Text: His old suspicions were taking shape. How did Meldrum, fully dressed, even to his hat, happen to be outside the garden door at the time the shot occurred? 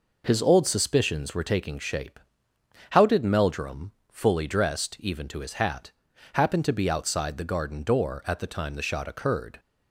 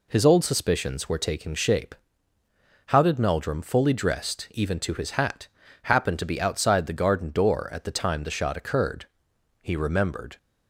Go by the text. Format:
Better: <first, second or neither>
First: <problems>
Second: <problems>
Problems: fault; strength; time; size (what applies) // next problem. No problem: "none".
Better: first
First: none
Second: goes on to say "He remembered"; noticeable; from 9.6 s on; 0.76 s long